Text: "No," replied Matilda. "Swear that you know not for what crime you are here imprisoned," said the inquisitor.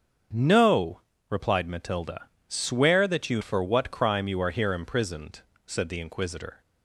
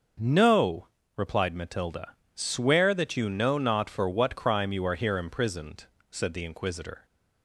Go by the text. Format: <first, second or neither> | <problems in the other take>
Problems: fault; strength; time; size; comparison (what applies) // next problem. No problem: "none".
second | starts louder than the rest; strong; until 1.6 s; 7 dB // skips "know not"; at 3.4 s